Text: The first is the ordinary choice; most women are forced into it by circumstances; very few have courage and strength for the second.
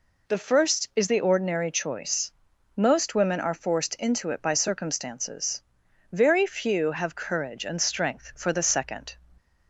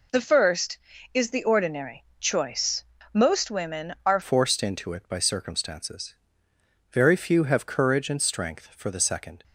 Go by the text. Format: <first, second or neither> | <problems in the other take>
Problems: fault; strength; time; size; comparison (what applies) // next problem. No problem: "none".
first | pauses between "ordinary" and "choice"; slight; at 2.0 s; 0.16 s long // changes voice at "forced"; from 4.2 s on; 5.2 s long